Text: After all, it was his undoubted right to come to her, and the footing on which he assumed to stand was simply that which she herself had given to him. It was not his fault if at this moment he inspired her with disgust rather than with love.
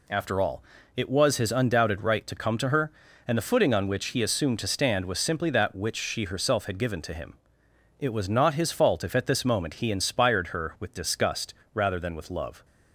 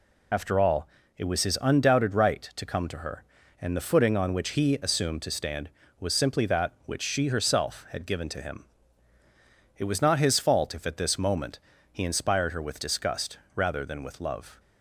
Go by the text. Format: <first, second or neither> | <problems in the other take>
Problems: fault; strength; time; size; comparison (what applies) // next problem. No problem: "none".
first | loses the start of "After"; at 0.3 s; 35 ms // pauses between "moment" and "he"; slight; at 11.5 s; 0.32 s long // pauses between "disgust" and "rather"; slight; at 13.3 s; 0.18 s long; slight in the first